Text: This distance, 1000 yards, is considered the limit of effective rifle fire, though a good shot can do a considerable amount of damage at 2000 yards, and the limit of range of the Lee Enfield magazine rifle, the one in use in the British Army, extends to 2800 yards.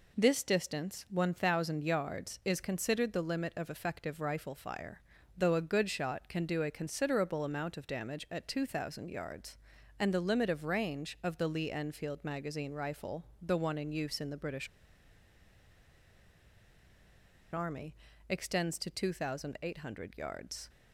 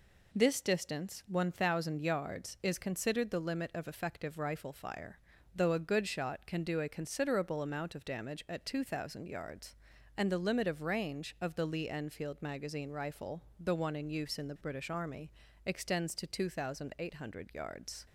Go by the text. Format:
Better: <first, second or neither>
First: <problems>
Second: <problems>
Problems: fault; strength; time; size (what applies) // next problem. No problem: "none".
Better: second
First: pauses between "British" and "Army"; strong; at 14.6 s; 2.8 s long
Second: none